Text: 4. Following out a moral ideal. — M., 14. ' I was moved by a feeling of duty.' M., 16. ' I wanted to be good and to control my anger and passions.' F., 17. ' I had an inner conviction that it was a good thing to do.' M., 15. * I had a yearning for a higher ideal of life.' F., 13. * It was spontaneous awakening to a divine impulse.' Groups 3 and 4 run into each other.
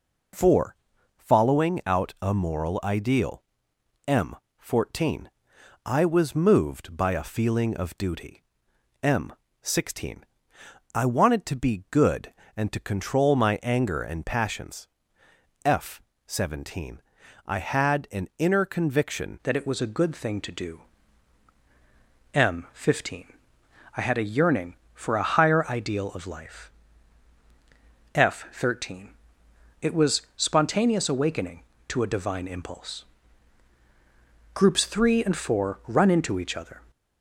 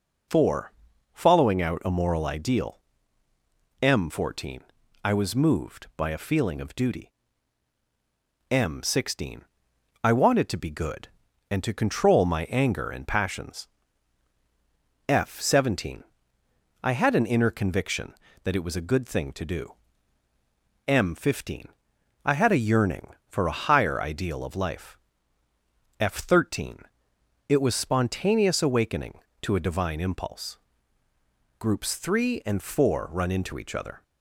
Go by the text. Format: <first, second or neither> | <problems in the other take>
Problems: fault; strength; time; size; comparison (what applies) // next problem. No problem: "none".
second | changes voice at "that"; from 19.4 s on; 17.4 s long // pauses between "was" and "spontaneous"; slight; at 30.2 s; 0.16 s long